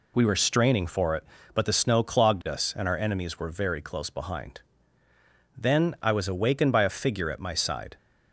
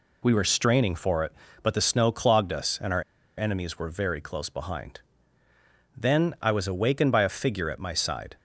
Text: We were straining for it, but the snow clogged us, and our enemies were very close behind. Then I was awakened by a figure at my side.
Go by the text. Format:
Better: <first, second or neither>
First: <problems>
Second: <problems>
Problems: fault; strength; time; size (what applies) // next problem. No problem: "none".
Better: first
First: none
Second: pauses between "our" and "enemies"; slight; at 3.0 s; 0.36 s long